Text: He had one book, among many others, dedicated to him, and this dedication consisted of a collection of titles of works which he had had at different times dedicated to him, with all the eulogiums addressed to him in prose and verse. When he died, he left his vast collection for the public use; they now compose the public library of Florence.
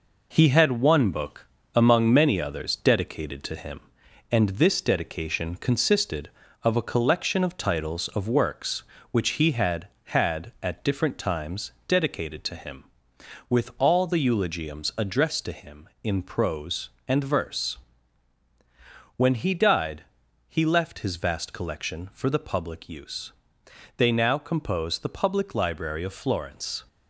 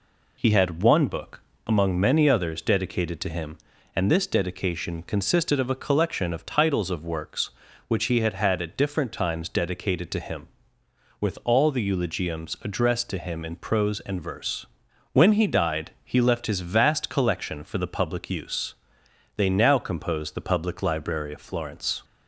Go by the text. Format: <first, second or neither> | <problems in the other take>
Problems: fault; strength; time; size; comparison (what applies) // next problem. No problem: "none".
second | gets quieter; noticeable; throughout; 4.5 dB